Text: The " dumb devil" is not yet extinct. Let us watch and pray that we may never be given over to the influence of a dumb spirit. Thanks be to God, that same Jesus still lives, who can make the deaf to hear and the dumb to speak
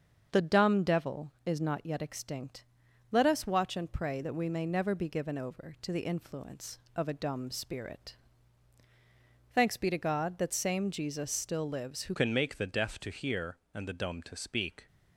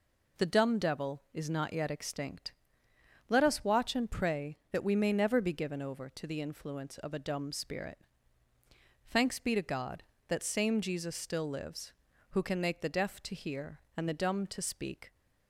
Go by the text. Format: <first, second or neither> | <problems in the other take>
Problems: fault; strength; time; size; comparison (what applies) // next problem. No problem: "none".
second | starts louder than the rest; until 1.3 s; 7 dB // changes voice at "can"; from 12.1 s on; 2.7 s long